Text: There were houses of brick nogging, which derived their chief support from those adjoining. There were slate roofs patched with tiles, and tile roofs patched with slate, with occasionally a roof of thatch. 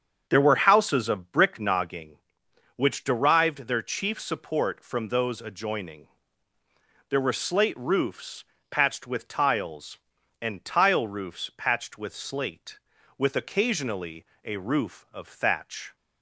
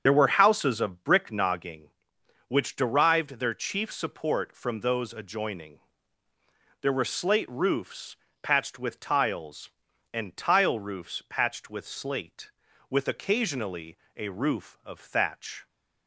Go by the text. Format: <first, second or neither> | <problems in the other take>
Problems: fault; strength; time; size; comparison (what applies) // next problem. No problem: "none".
first | loses the start of "There"; at 0.0 s; 45 ms // starts louder than the rest; strong; until 1.0 s; 7.5 dB; strong in the first // pauses between "roofs" and "patched"; slight; at 8.1 s; 0.28 s long; slight in the first // pauses between "occasionally" and "a"; slight; at 13.9 s; 0.18 s long; slight in the first